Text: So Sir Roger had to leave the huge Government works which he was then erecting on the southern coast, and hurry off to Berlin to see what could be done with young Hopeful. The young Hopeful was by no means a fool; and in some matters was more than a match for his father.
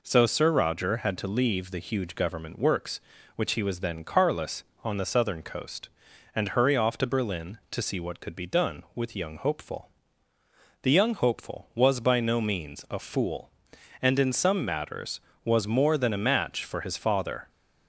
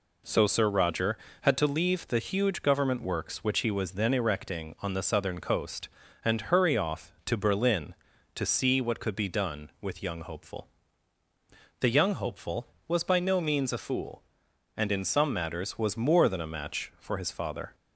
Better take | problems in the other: second | says "carless" for "erecting"; at 4.0 s

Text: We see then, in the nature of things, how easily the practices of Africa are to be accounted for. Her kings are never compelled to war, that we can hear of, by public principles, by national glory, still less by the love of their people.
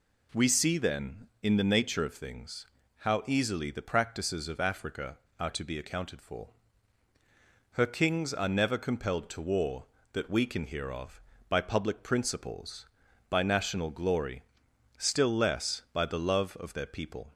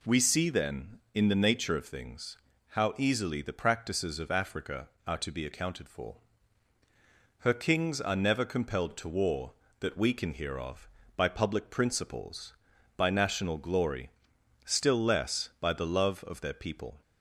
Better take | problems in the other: neither | none

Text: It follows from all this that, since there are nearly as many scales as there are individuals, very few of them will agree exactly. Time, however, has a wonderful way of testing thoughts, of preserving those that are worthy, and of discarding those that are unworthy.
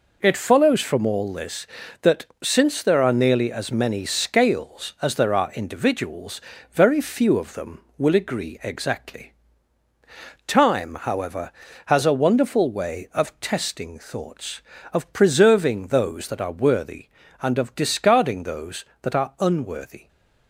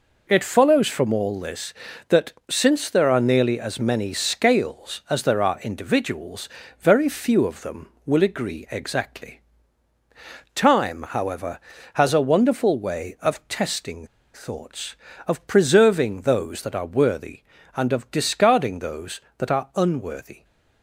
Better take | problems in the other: first | pauses between "testing" and "thoughts"; slight; at 14.0 s; 0.28 s long

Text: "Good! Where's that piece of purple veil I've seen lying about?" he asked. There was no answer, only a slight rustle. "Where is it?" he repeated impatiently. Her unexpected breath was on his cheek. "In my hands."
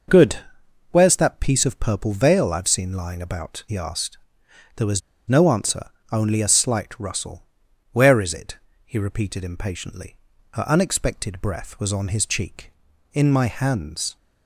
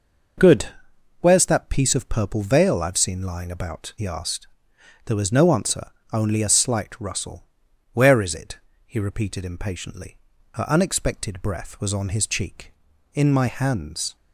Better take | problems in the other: second | pauses between "was" and "no"; slight; at 5.0 s; 0.29 s long

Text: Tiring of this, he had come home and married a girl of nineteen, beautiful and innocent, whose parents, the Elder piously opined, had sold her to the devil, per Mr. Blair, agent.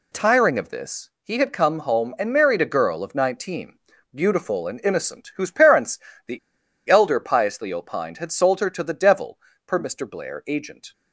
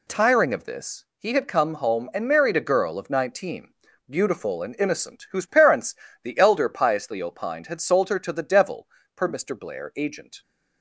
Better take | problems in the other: second | pauses between "the" and "Elder"; noticeable; at 6.3 s; 0.51 s long

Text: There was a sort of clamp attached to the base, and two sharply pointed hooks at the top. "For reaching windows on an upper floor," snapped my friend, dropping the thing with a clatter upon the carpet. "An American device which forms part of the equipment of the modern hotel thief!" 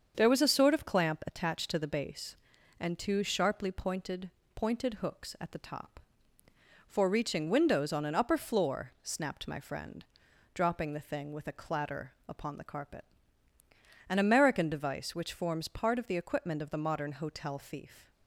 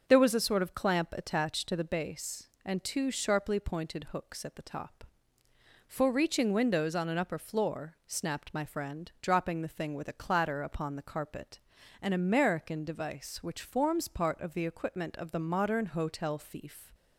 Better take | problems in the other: second | starts louder than the rest; until 1.1 s; 7 dB; also in the second // says "pointed" twice; at 4.5 s // pauses between "clatter" and "upon"; slight; at 12.1 s; 0.16 s long

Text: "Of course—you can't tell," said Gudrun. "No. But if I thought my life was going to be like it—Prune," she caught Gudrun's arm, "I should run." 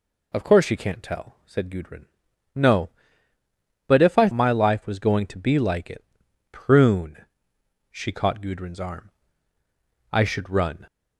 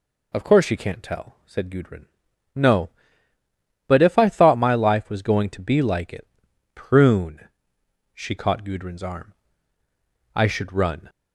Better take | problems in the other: second | skips "thought"; at 4.3 s

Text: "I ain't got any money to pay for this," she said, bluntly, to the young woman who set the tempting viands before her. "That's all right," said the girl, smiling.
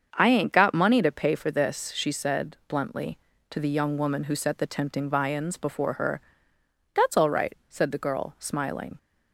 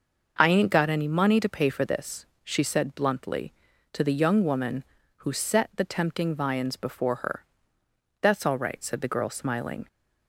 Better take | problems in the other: second | starts louder than the rest; until 1.1 s; 7 dB // skips "any"; at 0.7 s

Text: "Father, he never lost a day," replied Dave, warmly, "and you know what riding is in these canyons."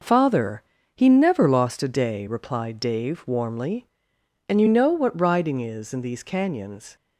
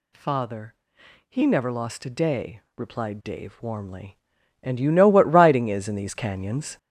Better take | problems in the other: first | gets louder; strong; throughout; 8.5 dB

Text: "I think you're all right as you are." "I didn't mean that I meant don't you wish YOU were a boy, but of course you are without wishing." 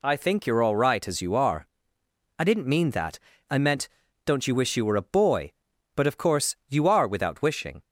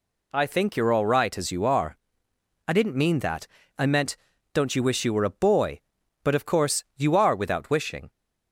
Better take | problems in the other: neither | pauses between "that" and "I"; slight; the same in both // pauses between "meant" and "don't"; the same in both

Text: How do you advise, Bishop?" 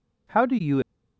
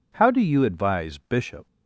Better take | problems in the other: second | stops before "advise Bishop"; at 0.8 s

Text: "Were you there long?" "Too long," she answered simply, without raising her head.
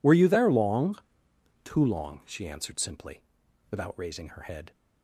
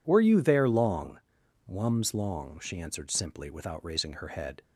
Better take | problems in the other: first | says "Wums" for "Too"; at 1.6 s

